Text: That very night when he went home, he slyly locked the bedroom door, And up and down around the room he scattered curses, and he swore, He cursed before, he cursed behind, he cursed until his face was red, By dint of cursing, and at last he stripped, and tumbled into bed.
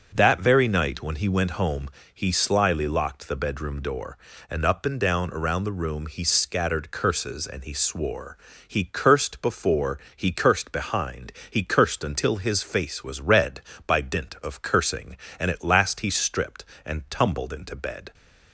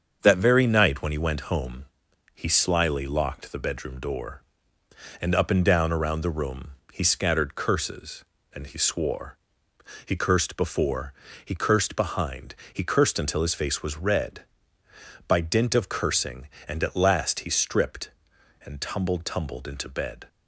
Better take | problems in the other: first | starts louder than the rest; until 1.2 s; 7 dB; strong in the first // pauses between "room" and "he"; slight; at 6.7 s; 0.20 s long // says "tumbled" twice; at 19.2 s

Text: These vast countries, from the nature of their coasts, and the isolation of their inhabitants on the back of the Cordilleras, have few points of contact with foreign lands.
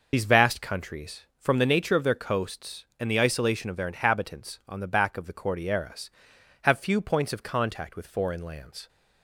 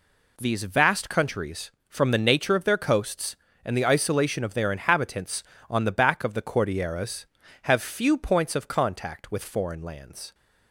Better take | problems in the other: second | loses the start of "These"; at 0.1 s; 55 ms

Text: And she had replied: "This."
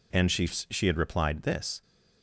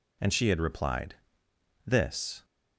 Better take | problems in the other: second | says "she" twice; at 0.4 s

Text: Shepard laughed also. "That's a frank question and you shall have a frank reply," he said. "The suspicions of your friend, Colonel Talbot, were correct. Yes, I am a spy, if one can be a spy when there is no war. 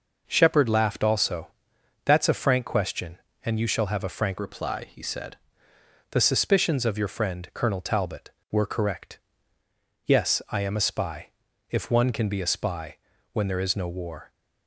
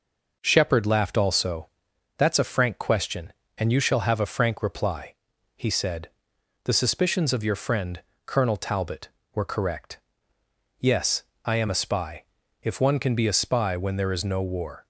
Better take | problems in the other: second | changes voice from "reply" to "said"; from 4.3 to 5.3 s; 1.0 s long // pauses between "spy" and "when"; slight; at 12.9 s; 0.36 s long

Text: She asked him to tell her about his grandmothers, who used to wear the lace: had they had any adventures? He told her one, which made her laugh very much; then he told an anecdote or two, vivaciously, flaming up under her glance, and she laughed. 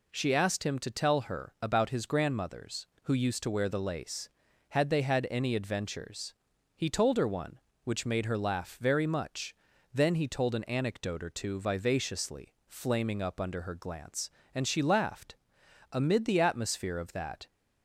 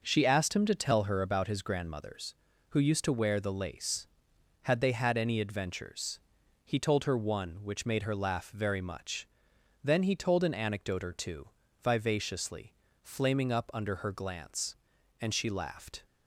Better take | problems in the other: second | goes on to say "Amid the atmosphere of that"; from 15.9 s on; 1.5 s long

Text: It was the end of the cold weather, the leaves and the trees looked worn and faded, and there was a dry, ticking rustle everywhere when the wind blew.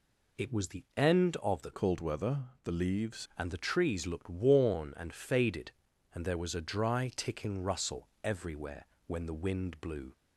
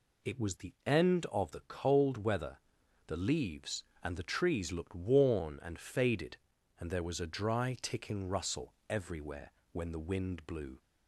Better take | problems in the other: second | changes voice from "cold" to "leaves"; from 1.7 to 3.2 s; 1.5 s long // pauses between "rustle" and "everywhere"; slight; at 8.0 s; 0.16 s long; slight in the second // pauses between "everywhere" and "when"; slight; at 8.8 s; 0.20 s long; slight in the second

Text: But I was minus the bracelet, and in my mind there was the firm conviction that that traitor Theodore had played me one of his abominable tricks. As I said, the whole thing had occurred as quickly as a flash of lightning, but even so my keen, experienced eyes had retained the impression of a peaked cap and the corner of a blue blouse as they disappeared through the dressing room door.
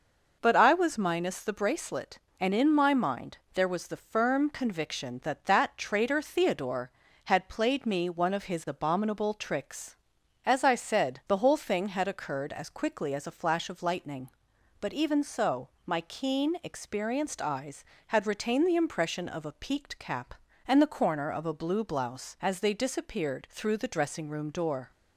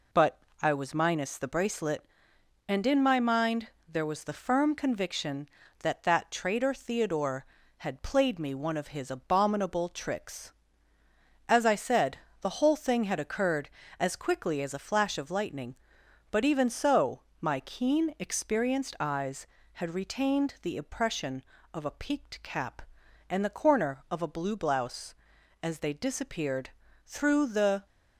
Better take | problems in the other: first | pauses between "But" and "I"; slight; at 0.3 s; 0.22 s long // pauses between "mind" and "there"; slight; at 3.6 s; 0.20 s long; slight in the first // pauses between "so" and "my"; slight; at 17.2 s; 0.18 s long; slight in the first // pauses between "disappeared" and "through"; slight; at 26.6 s; 0.36 s long // stops before "dressing room door"; at 27.8 s

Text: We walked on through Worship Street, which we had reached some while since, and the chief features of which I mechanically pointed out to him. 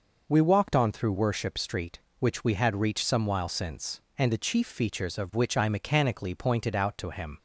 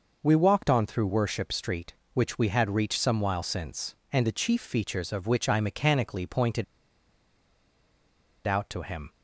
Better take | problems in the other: first | pauses between "pointed" and "out"; strong; at 6.6 s; 1.8 s long

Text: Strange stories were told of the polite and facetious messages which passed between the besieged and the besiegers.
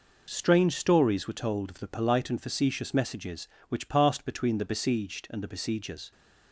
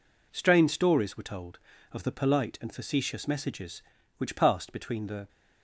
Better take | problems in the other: first | stops before "besieged and the besiegers"; at 5.2 s

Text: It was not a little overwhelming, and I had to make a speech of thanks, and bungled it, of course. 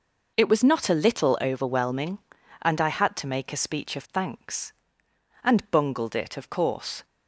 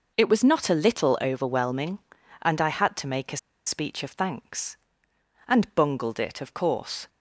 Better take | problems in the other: first | pauses between "a" and "speech"; slight; at 3.3 s; 0.29 s long

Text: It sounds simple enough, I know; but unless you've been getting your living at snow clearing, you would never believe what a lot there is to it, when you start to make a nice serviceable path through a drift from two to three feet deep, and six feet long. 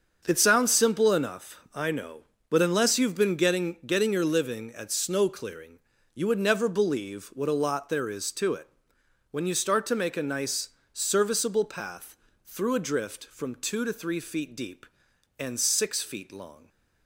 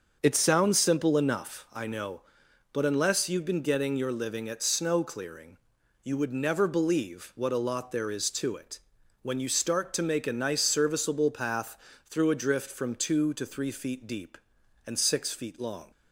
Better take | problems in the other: second | starts louder than the rest; until 1.2 s; 6.5 dB; also in the second // says "getting" twice; at 3.8 s // pauses between "nice" and "serviceable"; slight; at 10.6 s; 0.24 s long // pauses between "path" and "through"; slight; at 12.1 s; 0.28 s long; slight in the second

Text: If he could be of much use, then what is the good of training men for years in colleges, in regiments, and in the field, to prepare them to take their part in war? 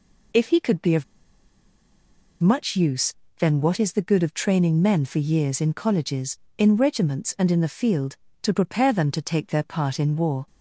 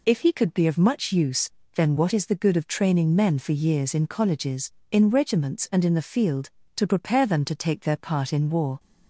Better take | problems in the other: second | pauses between "of" and "much"; strong; at 1.0 s; 1.3 s long

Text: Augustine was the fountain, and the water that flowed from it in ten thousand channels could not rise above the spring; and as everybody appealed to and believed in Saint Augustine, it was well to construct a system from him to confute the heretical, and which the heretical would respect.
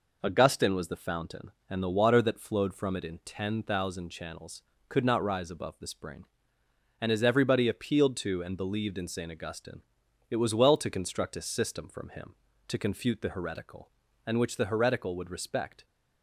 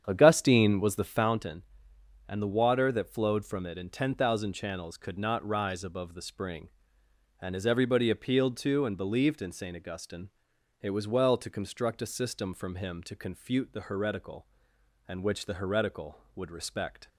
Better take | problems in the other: first | starts louder than the rest; strong; until 1.3 s; 8.5 dB

